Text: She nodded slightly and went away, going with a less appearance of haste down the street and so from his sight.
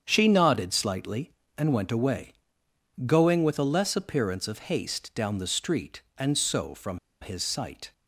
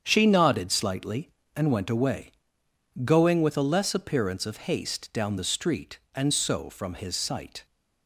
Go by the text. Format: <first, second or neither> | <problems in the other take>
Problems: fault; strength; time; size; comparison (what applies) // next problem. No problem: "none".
second | starts louder than the rest; strong; until 1.0 s; 8 dB; strong in the second // pauses between "from" and "his"; slight; at 6.9 s; 0.23 s long